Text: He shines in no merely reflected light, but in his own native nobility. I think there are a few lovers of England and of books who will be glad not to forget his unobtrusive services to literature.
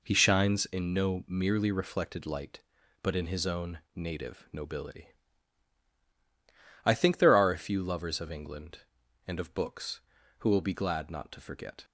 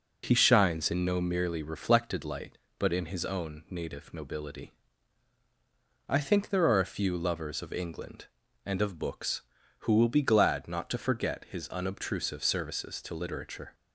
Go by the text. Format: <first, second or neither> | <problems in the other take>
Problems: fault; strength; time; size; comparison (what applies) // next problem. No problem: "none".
second | pauses between "own" and "native"; slight; at 3.7 s; 0.16 s long // stops before "his unobtrusive services to literature"; at 11.8 s